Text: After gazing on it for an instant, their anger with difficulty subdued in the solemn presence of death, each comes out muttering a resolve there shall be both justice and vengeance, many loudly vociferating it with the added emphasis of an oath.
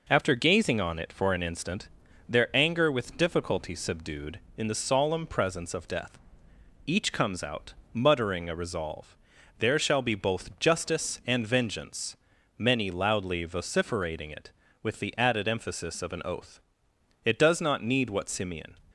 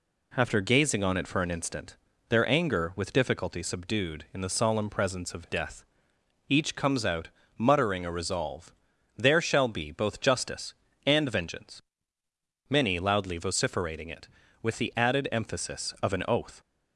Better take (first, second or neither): second